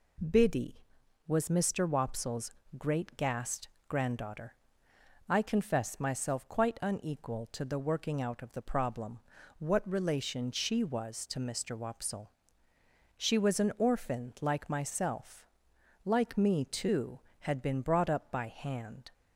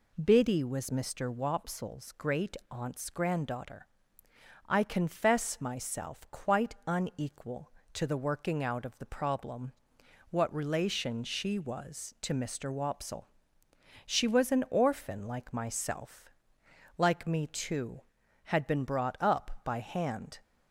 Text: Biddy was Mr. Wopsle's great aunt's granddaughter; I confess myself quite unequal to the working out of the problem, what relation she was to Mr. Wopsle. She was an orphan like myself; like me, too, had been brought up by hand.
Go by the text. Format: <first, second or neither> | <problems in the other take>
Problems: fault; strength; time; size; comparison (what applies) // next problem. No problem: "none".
second | pauses between "Wopsle's" and "great"; slight; at 2.5 s; 0.26 s long // says "gassed" for "aunt's"; at 3.1 s